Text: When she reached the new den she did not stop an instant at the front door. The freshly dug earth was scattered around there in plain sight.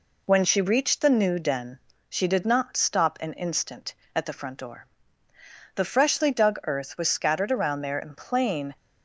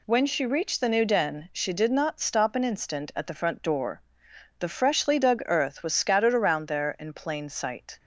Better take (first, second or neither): second